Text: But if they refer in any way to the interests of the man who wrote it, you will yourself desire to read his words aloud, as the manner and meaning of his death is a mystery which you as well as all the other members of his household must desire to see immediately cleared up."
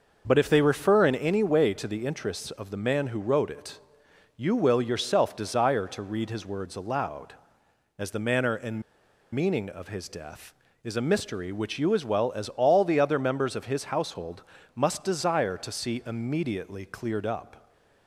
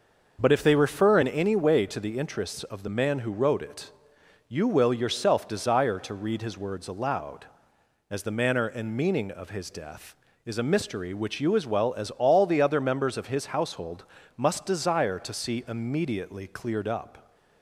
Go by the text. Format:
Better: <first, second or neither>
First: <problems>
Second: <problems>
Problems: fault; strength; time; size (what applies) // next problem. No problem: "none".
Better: second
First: pauses between "and" and "meaning"; noticeable; at 8.8 s; 0.52 s long // pauses between "household" and "must"; slight; at 14.4 s; 0.34 s long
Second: pauses between "household" and "must"; slight; at 14.0 s; 0.34 s long